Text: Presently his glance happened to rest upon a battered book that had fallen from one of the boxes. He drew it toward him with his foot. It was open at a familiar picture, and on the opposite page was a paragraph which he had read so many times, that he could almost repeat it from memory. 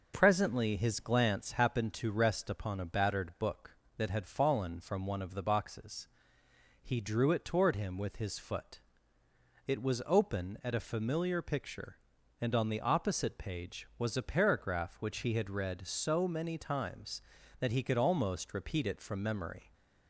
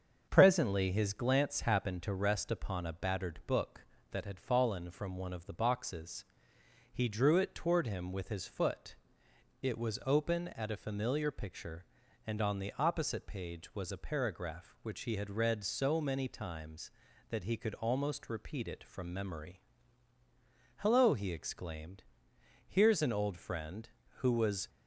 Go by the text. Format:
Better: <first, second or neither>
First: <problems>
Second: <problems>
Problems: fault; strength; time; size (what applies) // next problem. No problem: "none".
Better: first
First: none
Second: starts louder than the rest; until 1.2 s; 7 dB // goes on to say "Hello he exclaimed Here's an old friend who was"; strong; from 20.7 s on; 3.9 s long